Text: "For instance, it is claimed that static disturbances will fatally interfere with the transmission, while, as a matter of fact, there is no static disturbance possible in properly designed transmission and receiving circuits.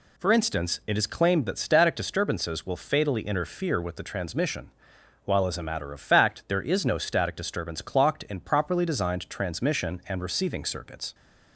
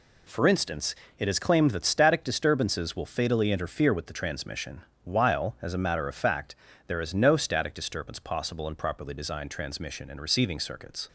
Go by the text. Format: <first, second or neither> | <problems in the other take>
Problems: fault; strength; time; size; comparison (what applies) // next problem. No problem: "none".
second | says "clocked" for "possible"; at 7.8 s